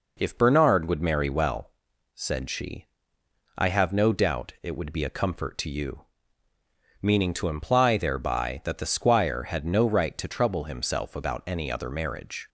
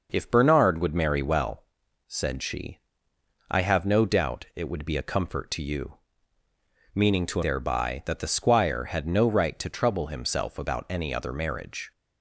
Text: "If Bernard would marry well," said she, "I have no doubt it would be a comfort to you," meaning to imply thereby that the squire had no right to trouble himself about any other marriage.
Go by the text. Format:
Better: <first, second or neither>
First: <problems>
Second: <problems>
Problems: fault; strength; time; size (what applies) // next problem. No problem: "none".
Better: first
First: none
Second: skips "imply"; at 7.4 s